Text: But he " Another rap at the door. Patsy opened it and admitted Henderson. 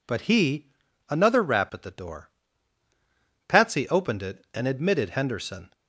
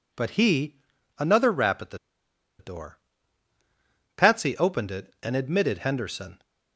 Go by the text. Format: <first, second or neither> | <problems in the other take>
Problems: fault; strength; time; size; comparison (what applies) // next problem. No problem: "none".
first | pauses between "the" and "door"; noticeable; at 1.9 s; 0.62 s long